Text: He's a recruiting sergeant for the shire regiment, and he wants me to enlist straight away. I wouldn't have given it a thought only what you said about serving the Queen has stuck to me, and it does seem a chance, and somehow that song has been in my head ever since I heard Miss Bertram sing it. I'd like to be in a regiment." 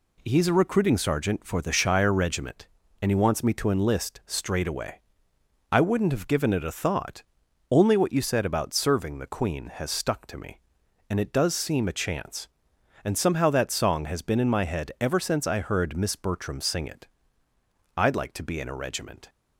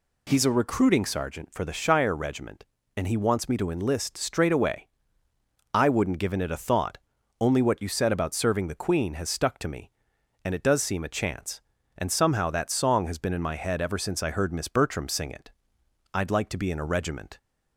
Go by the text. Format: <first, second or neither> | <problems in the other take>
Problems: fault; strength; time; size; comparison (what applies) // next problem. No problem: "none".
first | skips "have"; at 6.1 s // pauses between "thought" and "only"; at 6.9 s; 0.42 s long; noticeable in the first